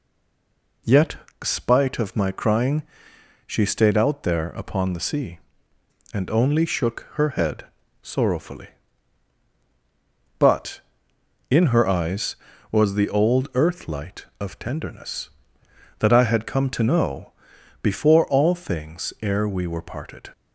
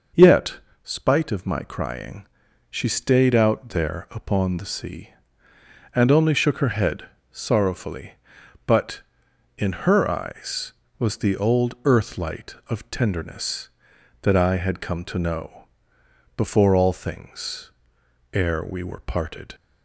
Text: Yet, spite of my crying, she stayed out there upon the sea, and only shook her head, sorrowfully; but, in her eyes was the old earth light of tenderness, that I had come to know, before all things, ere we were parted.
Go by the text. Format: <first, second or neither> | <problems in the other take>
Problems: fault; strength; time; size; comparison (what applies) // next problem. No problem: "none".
second | stays silent before the first word; slight; until 0.8 s; 0.8 s long